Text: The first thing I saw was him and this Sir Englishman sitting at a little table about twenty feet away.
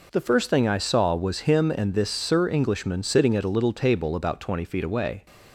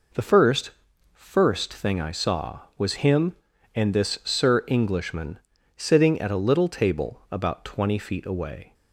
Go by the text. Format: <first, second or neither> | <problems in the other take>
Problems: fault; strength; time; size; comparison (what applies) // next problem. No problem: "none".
first | says "first" twice; at 1.1 s // pauses between "Englishman" and "sitting"; at 5.3 s; 0.38 s long